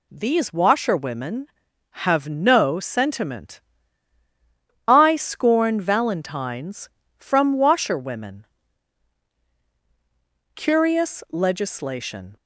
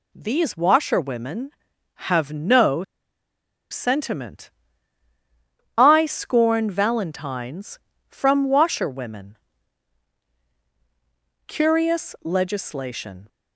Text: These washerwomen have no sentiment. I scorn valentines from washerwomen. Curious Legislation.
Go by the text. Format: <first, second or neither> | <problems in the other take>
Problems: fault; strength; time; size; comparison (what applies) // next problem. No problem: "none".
first | pauses between "no" and "sentiment"; noticeable; at 2.8 s; 0.88 s long